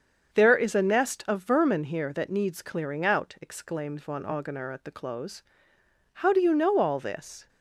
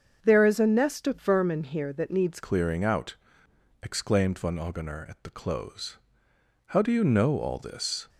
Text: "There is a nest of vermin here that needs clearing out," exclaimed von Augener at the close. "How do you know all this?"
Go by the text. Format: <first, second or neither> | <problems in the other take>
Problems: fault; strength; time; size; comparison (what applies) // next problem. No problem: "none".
first | starts louder than the rest; until 1.2 s; 7 dB; also in the first // changes voice at "clearing"; from 2.4 s on; 5.6 s long